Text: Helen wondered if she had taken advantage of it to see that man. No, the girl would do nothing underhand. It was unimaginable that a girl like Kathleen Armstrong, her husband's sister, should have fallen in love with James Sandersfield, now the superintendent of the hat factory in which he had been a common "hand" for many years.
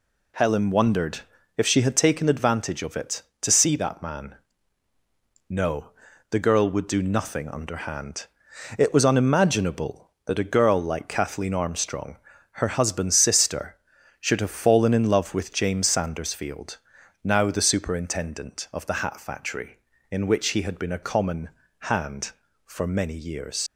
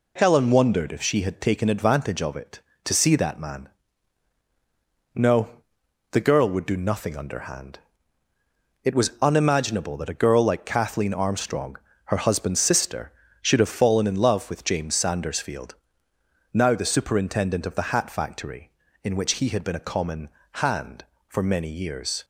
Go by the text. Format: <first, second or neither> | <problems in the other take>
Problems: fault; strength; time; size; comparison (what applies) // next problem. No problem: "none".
second | pauses between "wondered" and "if"; slight; at 1.2 s; 0.36 s long // pauses between "common" and "hand"; slight; at 21.4 s; 0.34 s long; slight in the second // leaves "years" unfinished; at 23.6 s; 105 ms